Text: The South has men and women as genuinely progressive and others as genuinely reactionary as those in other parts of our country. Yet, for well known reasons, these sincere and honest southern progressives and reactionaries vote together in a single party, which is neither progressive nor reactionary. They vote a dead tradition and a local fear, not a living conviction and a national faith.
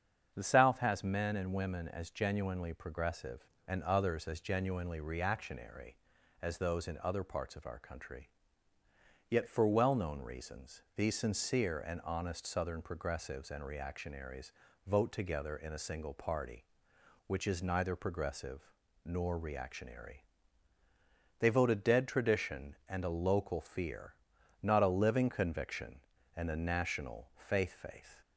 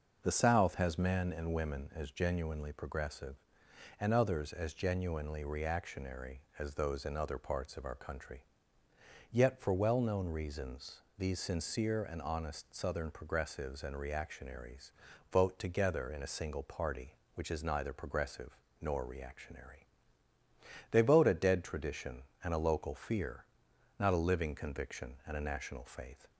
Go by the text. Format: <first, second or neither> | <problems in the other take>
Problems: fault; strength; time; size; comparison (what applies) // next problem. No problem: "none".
second | starts louder than the rest; strong; until 1.3 s; 7.5 dB // pauses between "reactionaries" and "vote"; slight; at 14.5 s; 0.34 s long; also in the second // pauses between "progressive" and "nor"; at 18.6 s; 0.44 s long; slight in the second // says "faith" twice; at 27.7 s